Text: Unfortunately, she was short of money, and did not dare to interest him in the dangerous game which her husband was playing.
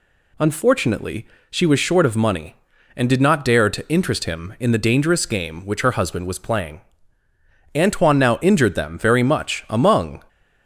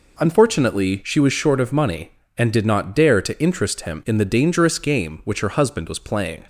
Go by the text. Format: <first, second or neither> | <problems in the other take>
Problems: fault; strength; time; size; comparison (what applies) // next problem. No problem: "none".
second | goes on to say "Antoine now injured them very much among"; strong; from 7.7 s on; 2.5 s long